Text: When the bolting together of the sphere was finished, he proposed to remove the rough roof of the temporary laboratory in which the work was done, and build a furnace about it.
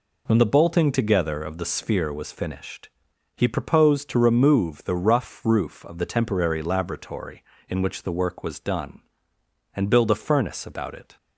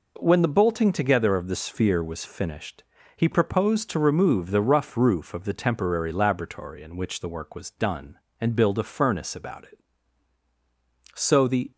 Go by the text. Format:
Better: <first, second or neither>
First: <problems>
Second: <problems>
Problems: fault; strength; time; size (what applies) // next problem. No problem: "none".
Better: first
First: none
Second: goes on to say "So the"; from 11.1 s on; 0.56 s long